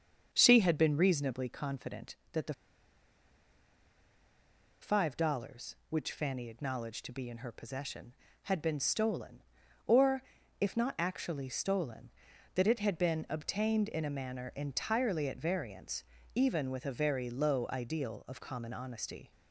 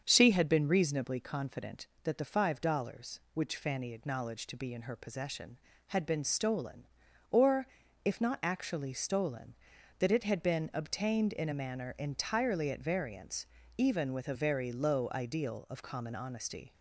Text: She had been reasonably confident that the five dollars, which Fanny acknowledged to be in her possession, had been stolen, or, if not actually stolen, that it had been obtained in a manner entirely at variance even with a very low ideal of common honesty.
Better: second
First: starts louder than the rest; strong; until 1.3 s; 7 dB // pauses between "the" and "five"; strong; at 2.5 s; 2.2 s long // pauses between "variance" and "even"; slight; at 16.0 s; 0.32 s long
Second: starts louder than the rest; strong; until 1.0 s; 7 dB // pauses between "variance" and "even"; slight; at 13.4 s; 0.32 s long

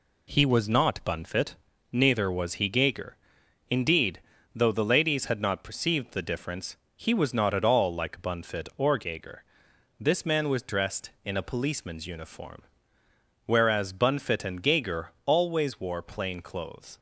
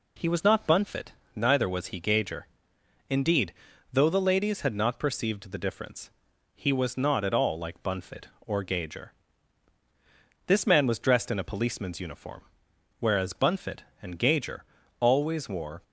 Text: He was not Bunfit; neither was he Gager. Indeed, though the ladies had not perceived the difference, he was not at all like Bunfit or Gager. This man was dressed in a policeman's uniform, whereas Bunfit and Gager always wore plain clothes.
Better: first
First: none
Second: pauses between "Gager" and "always"; slight; at 14.6 s; 0.36 s long // stops before "plain clothes"; at 15.8 s

